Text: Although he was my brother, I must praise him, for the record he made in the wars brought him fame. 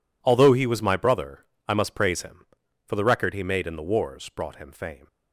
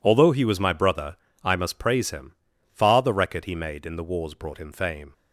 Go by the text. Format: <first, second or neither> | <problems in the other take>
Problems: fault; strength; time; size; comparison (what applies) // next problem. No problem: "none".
first | says "far" for "for"; at 2.7 s